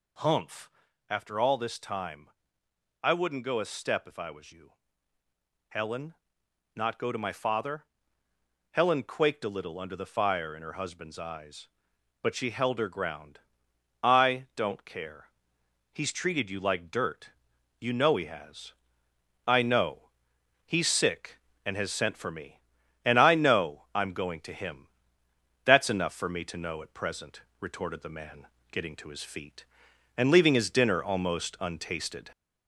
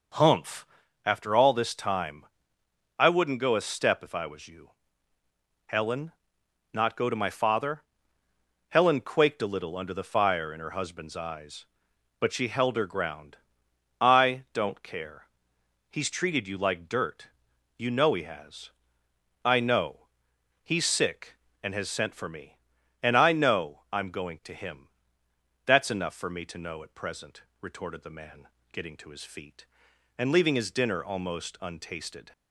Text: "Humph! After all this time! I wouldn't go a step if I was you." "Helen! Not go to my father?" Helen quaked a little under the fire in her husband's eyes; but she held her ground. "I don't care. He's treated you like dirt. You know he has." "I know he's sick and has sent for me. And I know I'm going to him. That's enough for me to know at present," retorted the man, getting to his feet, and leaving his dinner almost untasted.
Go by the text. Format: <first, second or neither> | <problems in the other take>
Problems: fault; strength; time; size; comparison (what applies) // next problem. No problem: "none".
second | gets louder; slight; throughout; 2 dB // pauses between "know" and "he's"; noticeable; at 20.1 s; 0.54 s long; noticeable in the second